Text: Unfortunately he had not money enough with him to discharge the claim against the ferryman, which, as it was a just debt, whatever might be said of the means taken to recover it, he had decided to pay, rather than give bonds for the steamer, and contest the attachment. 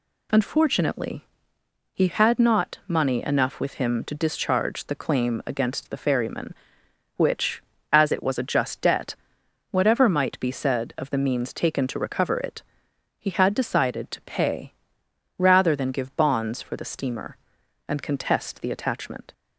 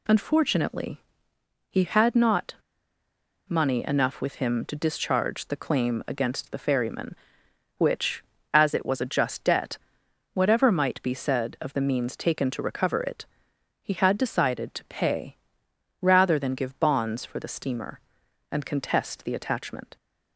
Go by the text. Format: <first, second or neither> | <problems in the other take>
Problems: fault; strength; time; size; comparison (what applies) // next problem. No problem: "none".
first | pauses between "Unfortunately" and "he"; noticeable; at 1.0 s; 0.68 s long; noticeable in the first // pauses between "not" and "money"; noticeable; at 2.5 s; 0.92 s long